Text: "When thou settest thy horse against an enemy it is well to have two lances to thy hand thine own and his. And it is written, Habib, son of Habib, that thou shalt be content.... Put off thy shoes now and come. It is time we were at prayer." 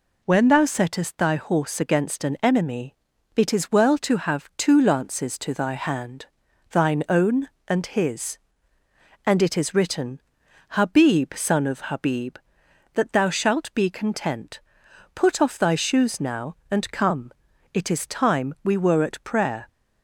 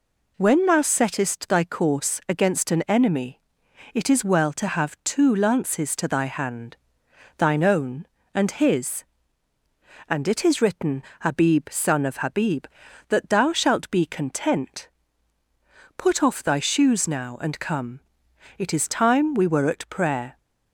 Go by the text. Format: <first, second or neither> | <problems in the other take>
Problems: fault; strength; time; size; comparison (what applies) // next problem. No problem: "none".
first | says "course" for "horse"; at 1.6 s // pauses between "enemy" and "it"; noticeable; at 3.4 s; 0.52 s long; also in the first // pauses between "hand" and "thine"; noticeable; at 6.7 s; 0.62 s long; also in the first